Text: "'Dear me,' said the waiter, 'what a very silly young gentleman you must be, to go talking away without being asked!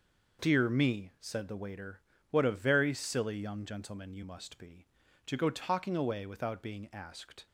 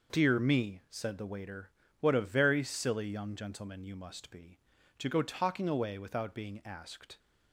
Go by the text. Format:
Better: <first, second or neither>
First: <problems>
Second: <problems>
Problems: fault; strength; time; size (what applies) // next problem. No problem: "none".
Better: neither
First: none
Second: none